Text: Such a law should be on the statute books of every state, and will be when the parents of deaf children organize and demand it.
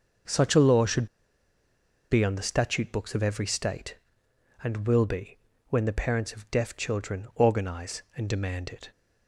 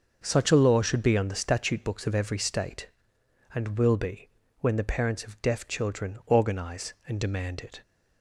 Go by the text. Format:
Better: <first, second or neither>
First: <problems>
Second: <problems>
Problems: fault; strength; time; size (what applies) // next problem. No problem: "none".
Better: second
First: starts louder than the rest; until 2.3 s; 6.5 dB // pauses between "should" and "be"; at 1.0 s; 1.0 s long // pauses between "be" and "when"; slight; at 5.3 s; 0.32 s long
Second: starts louder than the rest; until 1.2 s; 6.5 dB // pauses between "be" and "when"; slight; at 4.2 s; 0.32 s long